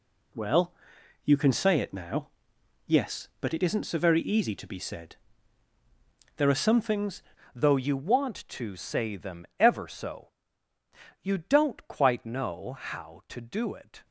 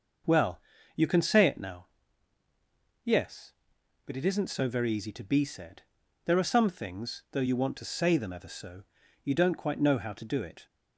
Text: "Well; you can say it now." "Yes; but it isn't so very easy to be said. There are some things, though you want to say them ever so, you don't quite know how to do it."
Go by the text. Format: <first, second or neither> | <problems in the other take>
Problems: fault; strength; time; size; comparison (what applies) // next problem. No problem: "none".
second | changes voice at "though"; from 7.5 s on; 6.5 s long